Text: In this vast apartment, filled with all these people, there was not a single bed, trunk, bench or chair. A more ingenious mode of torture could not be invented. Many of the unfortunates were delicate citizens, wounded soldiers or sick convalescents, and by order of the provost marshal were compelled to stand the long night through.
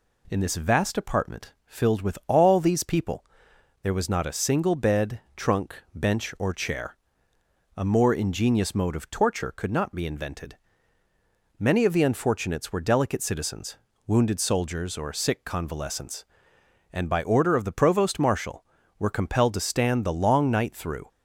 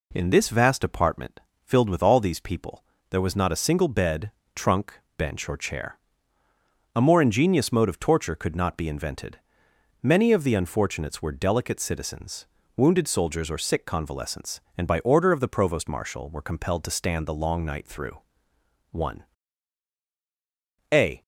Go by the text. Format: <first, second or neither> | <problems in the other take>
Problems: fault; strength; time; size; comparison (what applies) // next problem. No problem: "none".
first | goes on to say "One a"; strong; from 18.8 s on; 2.3 s long